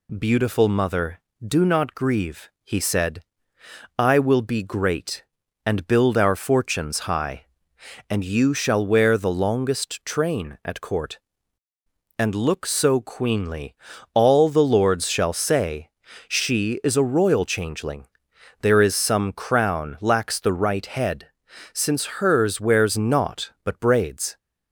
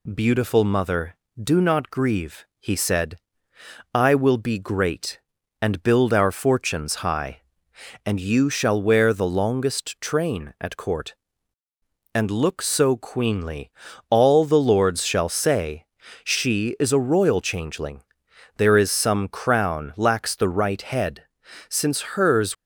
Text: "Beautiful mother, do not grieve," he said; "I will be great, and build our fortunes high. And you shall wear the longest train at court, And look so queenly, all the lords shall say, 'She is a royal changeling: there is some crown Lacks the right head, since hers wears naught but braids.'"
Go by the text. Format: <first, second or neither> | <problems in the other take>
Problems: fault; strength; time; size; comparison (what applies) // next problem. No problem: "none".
first | stops before "wears naught but braids"; at 22.5 s